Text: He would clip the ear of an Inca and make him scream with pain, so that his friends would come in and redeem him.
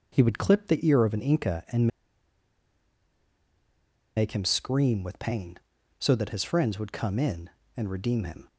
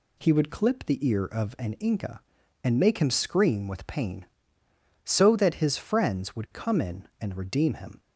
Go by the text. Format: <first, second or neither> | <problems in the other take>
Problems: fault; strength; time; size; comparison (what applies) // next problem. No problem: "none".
second | pauses between "and" and "make"; strong; at 1.8 s; 2.2 s long